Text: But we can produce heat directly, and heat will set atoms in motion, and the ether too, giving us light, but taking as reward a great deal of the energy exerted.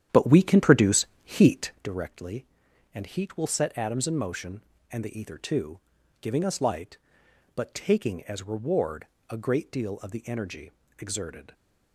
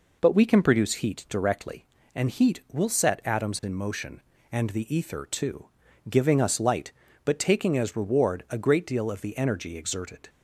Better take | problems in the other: second | starts louder than the rest; strong; until 1.9 s; 10 dB // pauses between "produce" and "heat"; slight; at 1.0 s; 0.18 s long // pauses between "reward" and "a"; slight; at 9.0 s; 0.24 s long // pauses between "energy" and "exerted"; slight; at 10.7 s; 0.26 s long

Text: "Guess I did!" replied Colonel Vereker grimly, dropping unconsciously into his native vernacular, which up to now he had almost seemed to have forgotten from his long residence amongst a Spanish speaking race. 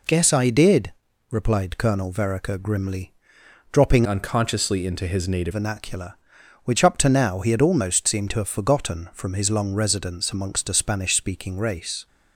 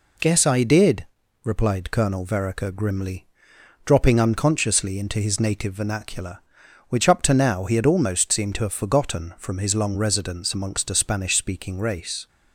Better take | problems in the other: second | changes voice from "unconsciously" to "native"; from 4.0 to 5.5 s; 1.5 s long

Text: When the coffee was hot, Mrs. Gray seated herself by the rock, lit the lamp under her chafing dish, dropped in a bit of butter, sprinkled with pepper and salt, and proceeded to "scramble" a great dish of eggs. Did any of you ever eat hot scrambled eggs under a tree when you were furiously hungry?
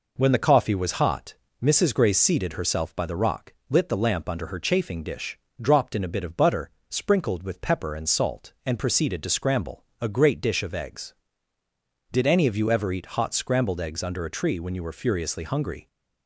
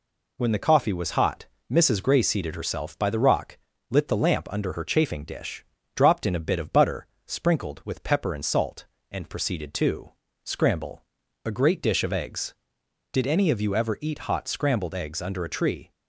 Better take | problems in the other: first | pauses between "to" and "scramble"; slight; at 10.1 s; 0.32 s long // pauses between "scramble" and "a"; at 11.0 s; 0.44 s long; slight in the first // stops before "when you were furiously hungry"; at 15.9 s

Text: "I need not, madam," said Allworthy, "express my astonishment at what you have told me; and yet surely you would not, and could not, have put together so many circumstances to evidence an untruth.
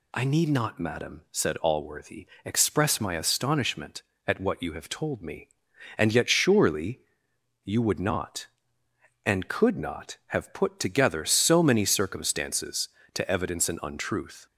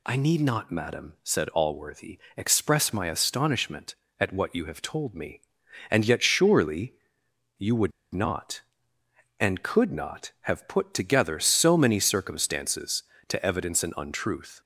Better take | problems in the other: first | pauses between "surely" and "you"; noticeable; at 6.9 s; 0.64 s long; noticeable in the first // pauses between "would" and "not"; slight; at 7.9 s; 0.20 s long

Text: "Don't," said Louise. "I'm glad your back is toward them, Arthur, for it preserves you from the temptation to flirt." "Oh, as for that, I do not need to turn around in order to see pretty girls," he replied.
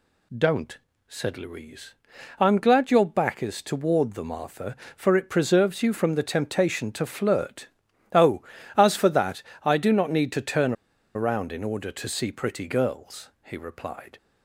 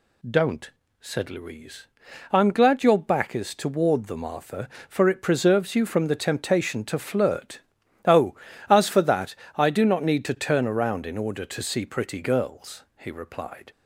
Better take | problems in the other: second | pauses between "turn" and "around"; at 10.7 s; 0.42 s long

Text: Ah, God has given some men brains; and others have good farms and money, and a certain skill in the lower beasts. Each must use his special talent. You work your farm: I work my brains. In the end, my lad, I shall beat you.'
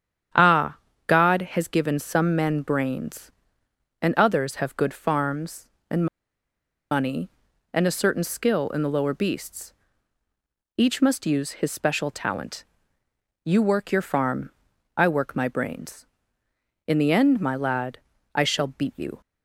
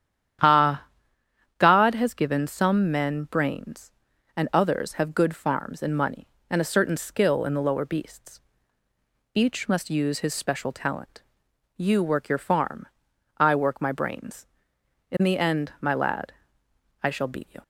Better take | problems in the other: second | starts louder than the rest; strong; until 1.6 s; 9 dB; strong in the second // pauses between "and" and "money"; noticeable; at 6.0 s; 0.85 s long

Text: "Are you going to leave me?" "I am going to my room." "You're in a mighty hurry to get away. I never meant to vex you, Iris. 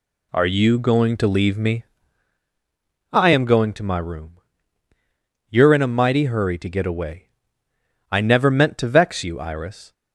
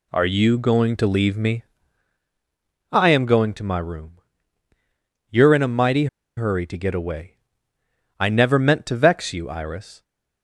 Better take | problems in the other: first | pauses between "mighty" and "hurry"; slight; at 6.0 s; 0.30 s long

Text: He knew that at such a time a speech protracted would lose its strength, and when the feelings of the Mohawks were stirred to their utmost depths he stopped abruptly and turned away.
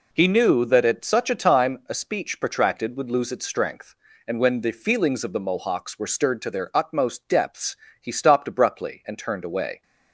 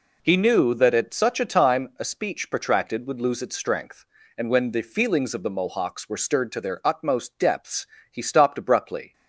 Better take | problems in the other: first | pauses between "depths" and "he"; slight; at 7.8 s; 0.26 s long; slight in the first // stops before "and turned away"; at 9.1 s

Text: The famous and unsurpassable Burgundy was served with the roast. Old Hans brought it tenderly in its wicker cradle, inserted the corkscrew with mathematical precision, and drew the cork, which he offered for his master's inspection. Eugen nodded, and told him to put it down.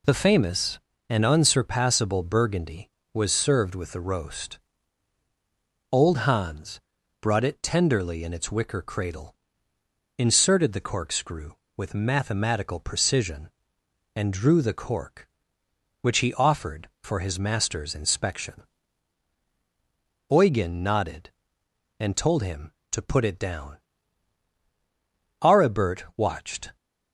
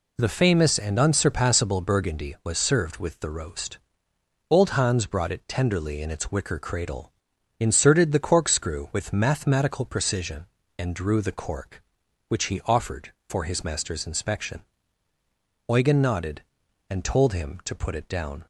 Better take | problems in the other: second | pauses between "Hans" and "brought"; at 6.7 s; 0.42 s long // goes on to say "Aribert watched"; from 25.4 s on; 1.3 s long

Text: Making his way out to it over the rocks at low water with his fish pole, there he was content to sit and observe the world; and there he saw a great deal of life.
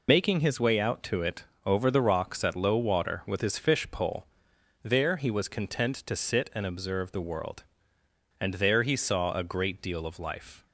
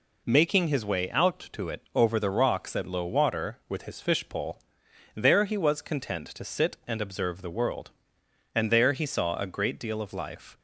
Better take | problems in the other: second | loses the start of "Making"; at 0.0 s; 65 ms // pauses between "it" and "over"; slight; at 1.4 s; 0.20 s long

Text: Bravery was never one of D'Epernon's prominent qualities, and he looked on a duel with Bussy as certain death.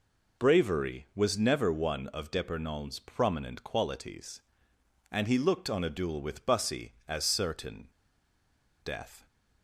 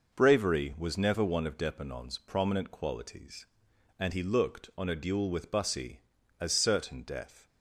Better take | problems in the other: second | pauses between "certain" and "death"; noticeable; at 7.8 s; 0.95 s long

